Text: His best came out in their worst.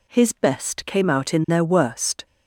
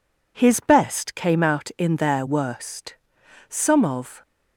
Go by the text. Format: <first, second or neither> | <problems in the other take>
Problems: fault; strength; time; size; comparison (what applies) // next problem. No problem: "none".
first | goes on to say "Some of"; noticeable; from 3.4 s on; 0.72 s long